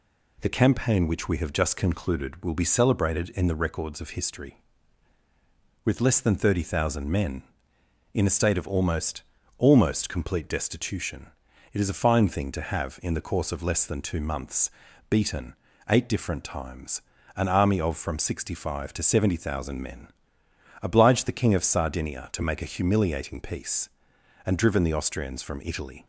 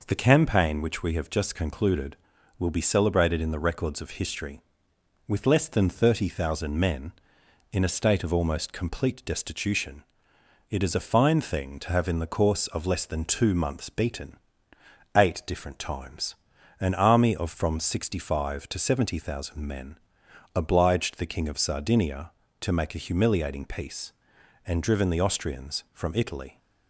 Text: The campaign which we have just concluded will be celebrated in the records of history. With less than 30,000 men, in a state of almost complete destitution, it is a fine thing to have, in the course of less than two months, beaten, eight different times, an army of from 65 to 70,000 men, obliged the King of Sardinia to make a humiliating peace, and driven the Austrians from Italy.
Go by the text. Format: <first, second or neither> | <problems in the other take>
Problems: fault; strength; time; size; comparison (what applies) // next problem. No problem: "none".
second | says "almost" twice; at 9.5 s